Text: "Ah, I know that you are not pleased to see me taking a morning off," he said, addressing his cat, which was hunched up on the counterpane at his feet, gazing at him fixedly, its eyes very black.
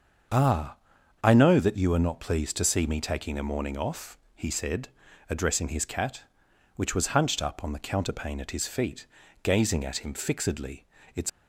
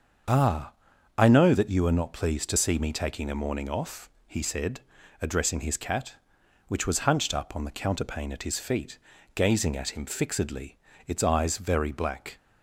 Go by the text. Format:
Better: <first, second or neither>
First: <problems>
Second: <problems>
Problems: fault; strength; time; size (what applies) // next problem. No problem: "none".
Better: second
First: starts louder than the rest; until 1.7 s; 7 dB // stops before "eyes very black"; at 11.2 s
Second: starts louder than the rest; until 1.7 s; 7 dB